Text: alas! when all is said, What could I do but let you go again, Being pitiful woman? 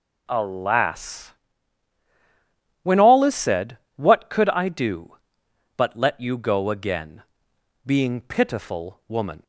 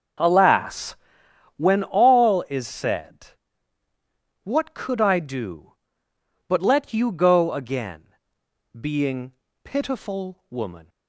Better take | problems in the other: first | starts louder than the rest; until 1.4 s; 6 dB // pauses between "Being" and "pitiful"; slight; at 9.3 s; 0.30 s long

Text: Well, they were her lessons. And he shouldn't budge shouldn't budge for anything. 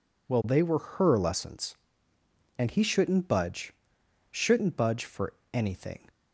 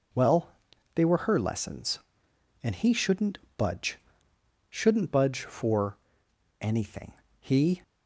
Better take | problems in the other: first | pauses between "shouldn't" and "budge"; slight; at 3.3 s; 0.18 s long // pauses between "budge" and "shouldn't"; noticeable; at 3.9 s; 0.72 s long; noticeable in the first // pauses between "for" and "anything"; noticeable; at 5.9 s; 0.64 s long; slight in the first // goes on to say "He"; slight; from 7.4 s on; 0.42 s long

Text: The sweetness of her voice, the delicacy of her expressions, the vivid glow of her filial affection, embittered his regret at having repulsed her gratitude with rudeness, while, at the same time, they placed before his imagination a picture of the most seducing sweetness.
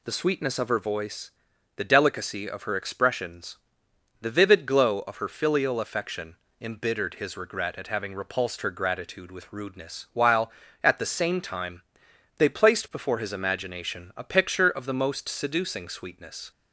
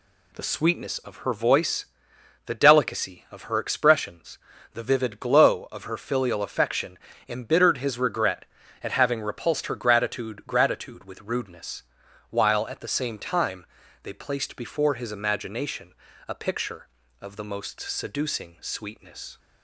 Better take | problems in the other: first | says "gratitude" twice; at 10.4 s // pauses between "imagination" and "a"; slight; at 15.9 s; 0.34 s long

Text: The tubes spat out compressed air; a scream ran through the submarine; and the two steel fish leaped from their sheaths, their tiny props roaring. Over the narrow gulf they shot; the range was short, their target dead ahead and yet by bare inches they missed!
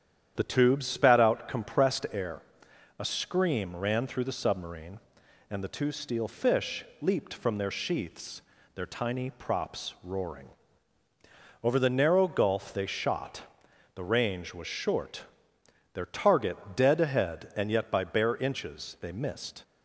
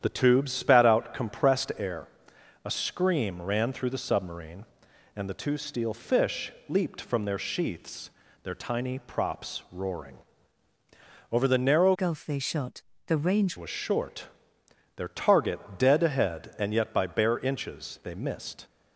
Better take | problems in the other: first | starts louder than the rest; strong; until 1.0 s; 9.5 dB; strong in the first // pauses between "fish" and "leaped"; slight; at 6.5 s; 0.18 s long; slight in the first // changes voice from "gulf" to "range"; from 11.9 to 13.5 s; 1.6 s long // pauses between "target" and "dead"; slight; at 15.6 s; 0.16 s long; slight in the first

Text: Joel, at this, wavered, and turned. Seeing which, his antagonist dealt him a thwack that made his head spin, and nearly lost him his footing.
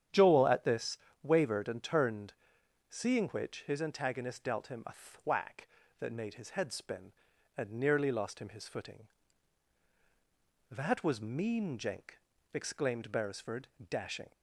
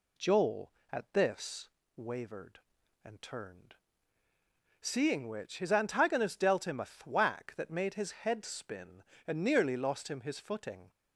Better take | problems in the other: second | starts louder than the rest; strong; until 1.3 s; 9.5 dB // goes on to say "That was mean Jenk exclaimed Beresford dashing"; strong; from 10.7 s on; 3.6 s long

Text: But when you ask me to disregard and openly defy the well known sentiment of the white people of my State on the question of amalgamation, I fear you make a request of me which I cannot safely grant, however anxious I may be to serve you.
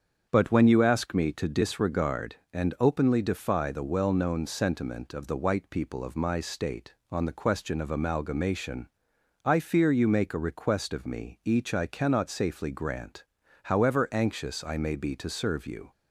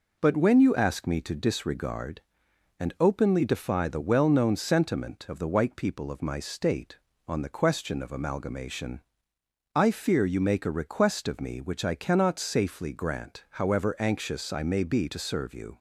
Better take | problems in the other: second | starts louder than the rest; strong; until 1.3 s; 7 dB // says "each" for "which"; at 11.4 s

